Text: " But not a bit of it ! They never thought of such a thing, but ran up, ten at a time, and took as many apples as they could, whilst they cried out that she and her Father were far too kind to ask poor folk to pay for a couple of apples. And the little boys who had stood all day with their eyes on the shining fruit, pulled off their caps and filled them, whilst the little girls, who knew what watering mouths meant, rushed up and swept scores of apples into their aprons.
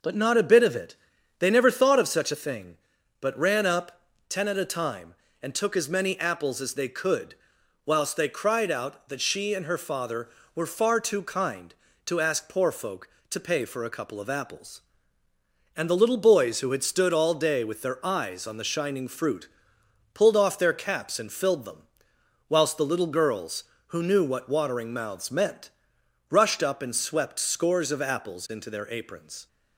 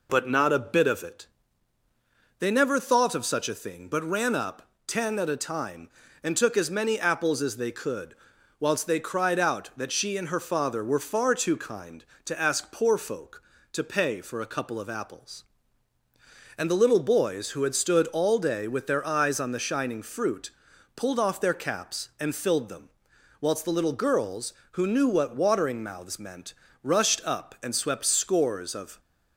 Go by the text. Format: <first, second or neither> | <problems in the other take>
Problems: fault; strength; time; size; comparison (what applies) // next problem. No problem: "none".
first | stops before "apples into their aprons"; at 28.9 s